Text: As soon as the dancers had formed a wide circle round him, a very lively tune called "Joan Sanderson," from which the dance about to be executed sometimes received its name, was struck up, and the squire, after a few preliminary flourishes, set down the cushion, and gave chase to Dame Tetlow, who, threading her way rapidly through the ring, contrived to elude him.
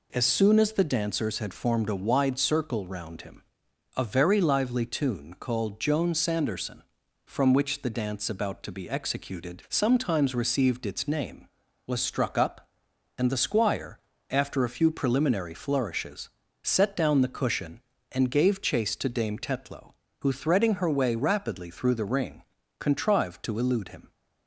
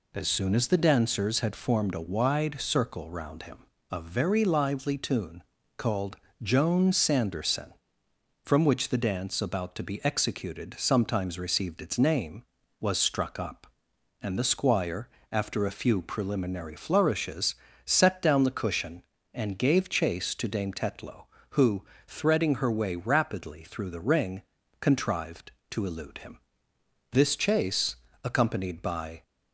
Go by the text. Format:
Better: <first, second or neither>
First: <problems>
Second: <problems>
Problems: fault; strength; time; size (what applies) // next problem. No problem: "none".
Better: first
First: none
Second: pauses between "tune" and "called"; slight; at 5.4 s; 0.36 s long // pauses between "called" and "Joan"; slight; at 6.1 s; 0.24 s long // goes on to say "This chase accompanied by"; strong; from 27.1 s on; 2.1 s long